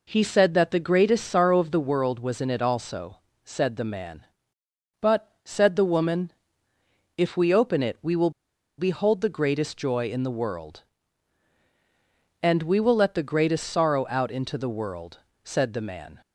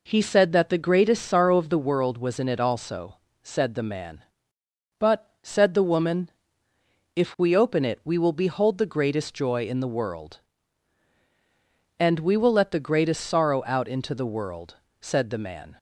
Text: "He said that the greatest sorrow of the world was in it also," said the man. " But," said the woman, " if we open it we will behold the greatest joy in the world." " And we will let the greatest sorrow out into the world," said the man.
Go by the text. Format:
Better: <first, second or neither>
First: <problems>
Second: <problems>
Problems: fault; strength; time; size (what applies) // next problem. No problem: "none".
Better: second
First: pauses between "will" and "behold"; noticeable; at 8.3 s; 0.48 s long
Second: none